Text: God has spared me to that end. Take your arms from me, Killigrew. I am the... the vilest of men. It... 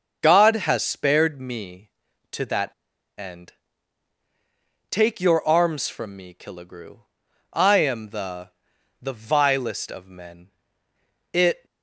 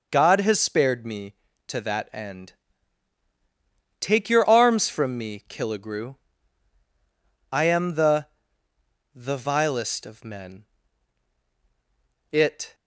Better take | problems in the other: second | starts louder than the rest; until 1.2 s; 6 dB // pauses between "that" and "end"; at 2.7 s; 0.45 s long

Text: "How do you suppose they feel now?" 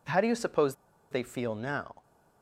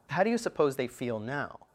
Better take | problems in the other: second | pauses between "suppose" and "they"; at 0.7 s; 0.37 s long

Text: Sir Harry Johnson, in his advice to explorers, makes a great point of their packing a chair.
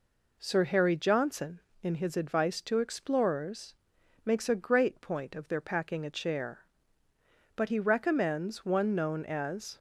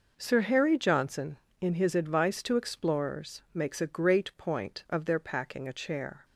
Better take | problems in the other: second | goes on to say "But he recommends one known as"; strong; from 7.5 s on; 2.2 s long

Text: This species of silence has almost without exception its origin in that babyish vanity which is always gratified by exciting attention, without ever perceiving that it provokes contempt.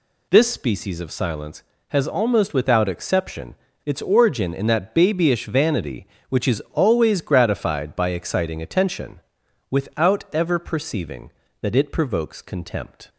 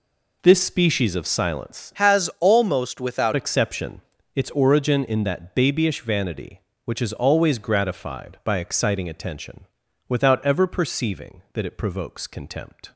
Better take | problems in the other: first | changes voice from "has" to "without"; from 1.9 to 3.3 s; 1.4 s long // pauses between "exception" and "its"; slight; at 4.0 s; 0.36 s long; slight in the first

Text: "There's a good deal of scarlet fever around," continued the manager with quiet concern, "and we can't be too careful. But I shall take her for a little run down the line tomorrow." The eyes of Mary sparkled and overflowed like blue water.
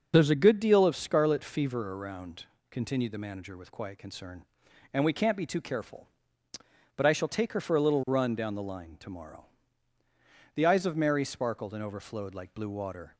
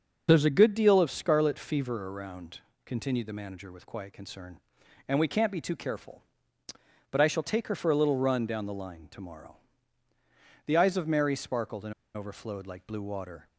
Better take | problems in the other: first | starts louder than the rest; noticeable; until 1.3 s; 6 dB; noticeable in the first // pauses between "and" and "overflowed"; slight; at 11.9 s; 0.23 s long

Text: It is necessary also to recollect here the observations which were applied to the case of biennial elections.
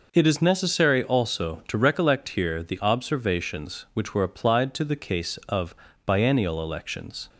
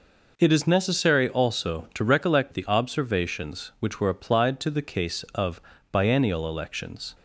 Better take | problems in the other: first | skips "here"; at 2.5 s // pauses between "of" and "biennial"; slight; at 5.6 s; 0.32 s long; slight in the first

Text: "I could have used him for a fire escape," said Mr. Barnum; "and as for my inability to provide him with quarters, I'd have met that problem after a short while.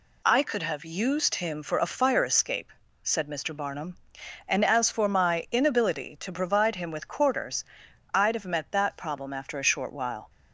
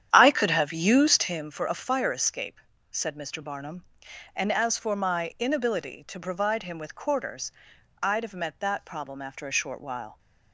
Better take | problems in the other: first | starts louder than the rest; strong; until 1.4 s; 9.5 dB

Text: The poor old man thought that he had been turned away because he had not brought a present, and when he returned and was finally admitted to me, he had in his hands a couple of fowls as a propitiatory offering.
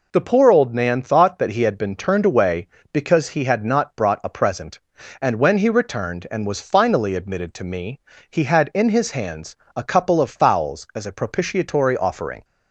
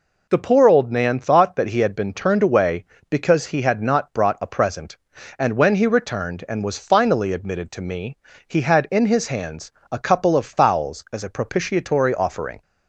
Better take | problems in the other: neither | pauses between "hands" and "a"; slight; the same in both

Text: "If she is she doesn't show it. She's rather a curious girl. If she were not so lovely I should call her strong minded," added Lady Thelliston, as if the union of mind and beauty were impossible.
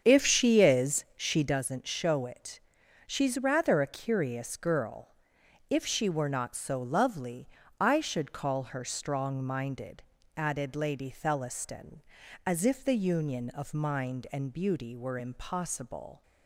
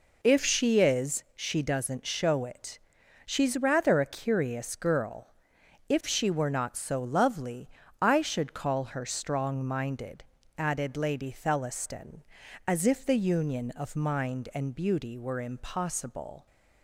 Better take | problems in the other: second | starts louder than the rest; strong; until 1.6 s; 7.5 dB // pauses between "lovely" and "I"; slight; at 7.4 s; 0.32 s long; slight in the second

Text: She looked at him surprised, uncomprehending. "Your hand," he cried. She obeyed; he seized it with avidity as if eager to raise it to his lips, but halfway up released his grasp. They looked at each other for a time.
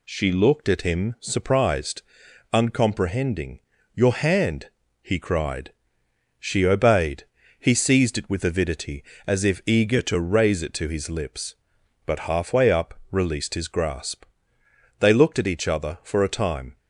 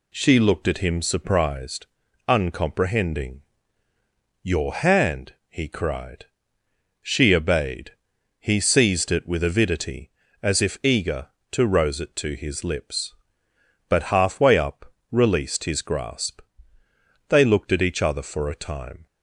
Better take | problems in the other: first | says "rose" for "raise"; at 11.6 s // pauses between "up" and "released"; slight; at 14.9 s; 0.18 s long

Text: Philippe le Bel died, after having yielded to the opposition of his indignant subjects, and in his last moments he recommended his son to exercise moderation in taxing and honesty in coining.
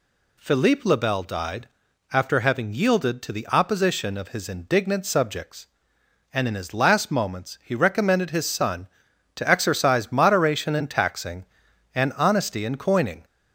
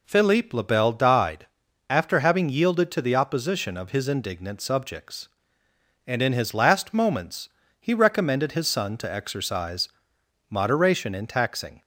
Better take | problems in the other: first | pauses between "moments" and "he"; slight; at 7.4 s; 0.30 s long // pauses between "exercise" and "moderation"; noticeable; at 9.8 s; 0.62 s long // stops before "and honesty in coining"; at 11.8 s

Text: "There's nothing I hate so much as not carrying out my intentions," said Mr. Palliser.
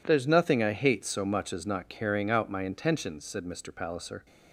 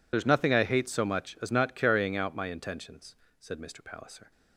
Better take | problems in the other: first | loses the start of "There's"; at 0.1 s; 75 ms

